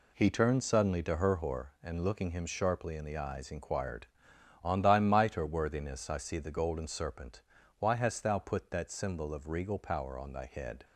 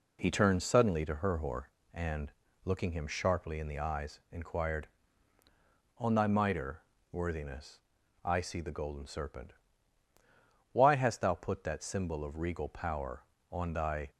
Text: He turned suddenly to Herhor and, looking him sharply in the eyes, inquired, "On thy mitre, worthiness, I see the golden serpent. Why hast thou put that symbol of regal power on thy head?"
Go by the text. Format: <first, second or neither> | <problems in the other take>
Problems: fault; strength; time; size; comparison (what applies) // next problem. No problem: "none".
first | stops before "head"; at 14.0 s